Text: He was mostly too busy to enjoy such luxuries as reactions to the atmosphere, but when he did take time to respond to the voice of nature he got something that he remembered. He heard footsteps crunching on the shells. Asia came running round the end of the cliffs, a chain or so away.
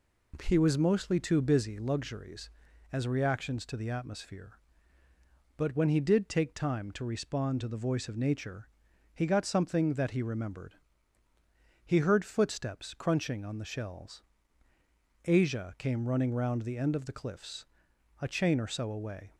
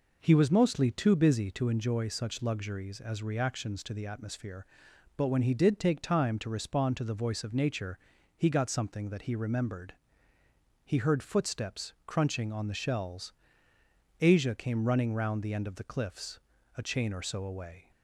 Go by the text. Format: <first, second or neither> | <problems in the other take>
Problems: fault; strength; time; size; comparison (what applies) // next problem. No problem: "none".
second | skips "to enjoy such"; at 1.7 s // pauses between "nature" and "he"; noticeable; at 8.6 s; 0.46 s long; also in the second